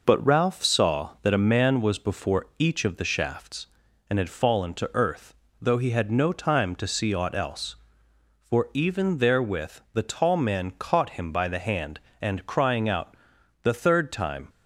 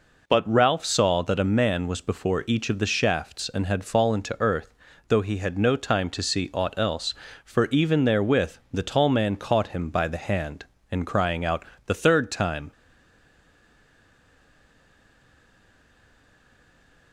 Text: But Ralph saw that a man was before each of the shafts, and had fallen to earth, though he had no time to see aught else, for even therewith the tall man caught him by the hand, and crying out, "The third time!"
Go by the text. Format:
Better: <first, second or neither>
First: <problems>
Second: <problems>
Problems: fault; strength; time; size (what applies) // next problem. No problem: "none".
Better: first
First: none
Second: pauses between "therewith" and "the"; slight; at 8.5 s; 0.18 s long // stays silent after the last word; strong; from 12.7 s on; 4.4 s long